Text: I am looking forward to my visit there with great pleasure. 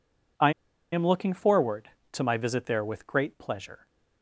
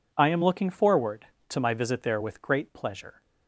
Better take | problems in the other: second | pauses between "I" and "am"; at 0.5 s; 0.41 s long

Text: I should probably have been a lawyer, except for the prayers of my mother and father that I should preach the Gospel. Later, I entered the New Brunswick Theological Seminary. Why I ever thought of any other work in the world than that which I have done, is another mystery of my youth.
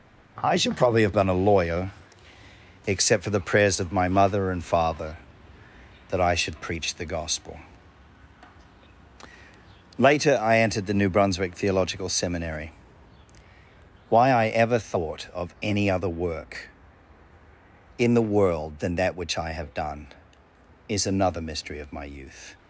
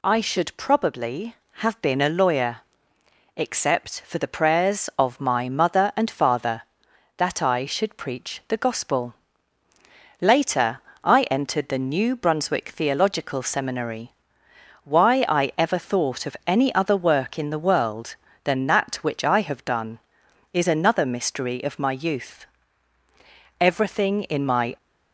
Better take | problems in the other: first | goes on to say "Everything in my"; noticeable; from 23.6 s on; 1.1 s long

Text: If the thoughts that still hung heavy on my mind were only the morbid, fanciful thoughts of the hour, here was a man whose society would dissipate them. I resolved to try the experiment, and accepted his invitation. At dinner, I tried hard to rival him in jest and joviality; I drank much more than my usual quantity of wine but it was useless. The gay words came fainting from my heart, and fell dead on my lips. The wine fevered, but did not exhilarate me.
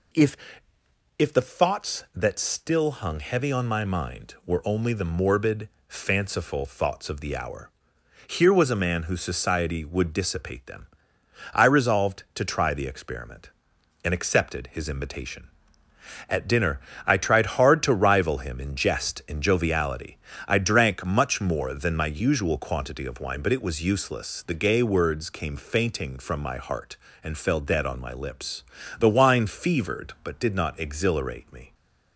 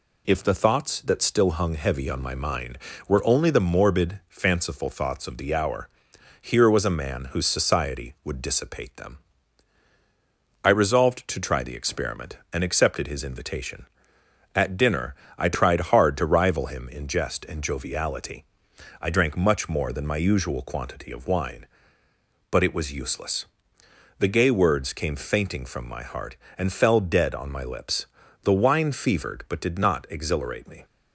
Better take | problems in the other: second | says "If" twice; at 1.1 s

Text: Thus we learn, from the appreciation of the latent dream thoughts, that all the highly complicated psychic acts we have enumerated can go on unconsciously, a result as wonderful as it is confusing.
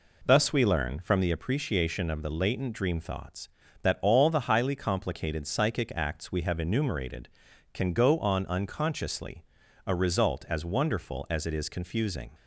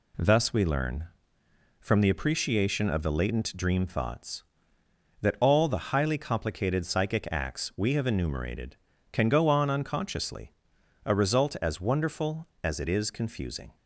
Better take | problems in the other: neither | none

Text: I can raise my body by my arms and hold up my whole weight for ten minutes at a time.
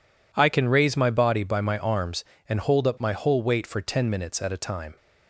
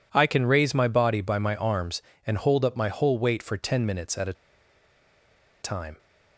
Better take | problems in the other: first | pauses between "a" and "time"; strong; at 4.3 s; 1.2 s long

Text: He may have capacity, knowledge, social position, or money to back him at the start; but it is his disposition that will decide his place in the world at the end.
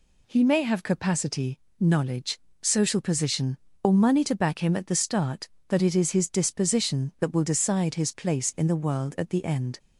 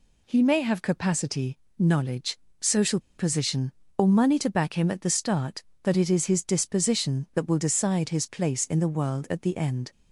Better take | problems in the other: first | pauses between "social" and "position"; slight; at 2.9 s; 0.18 s long

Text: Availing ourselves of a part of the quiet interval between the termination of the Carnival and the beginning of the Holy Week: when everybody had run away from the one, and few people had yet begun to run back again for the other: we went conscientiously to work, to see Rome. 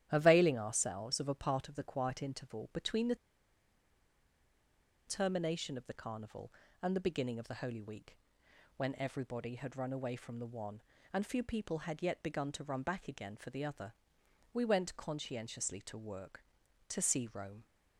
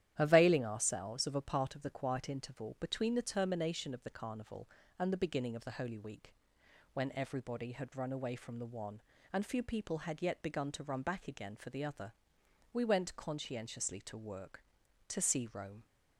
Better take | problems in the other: second | starts louder than the rest; strong; until 1.1 s; 11.5 dB; strong in the second // pauses between "the" and "termination"; strong; at 3.1 s; 1.9 s long

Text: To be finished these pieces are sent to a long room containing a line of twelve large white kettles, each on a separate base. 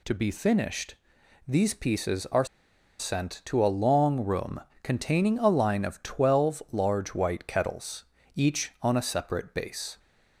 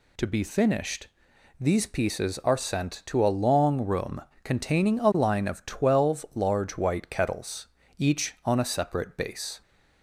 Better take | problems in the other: second | pauses between "finished" and "these"; noticeable; at 0.9 s; 0.52 s long; noticeable in the second // pauses between "are" and "sent"; noticeable; at 2.4 s; 0.54 s long // pauses between "room" and "containing"; slight; at 4.6 s; 0.20 s long; slight in the second

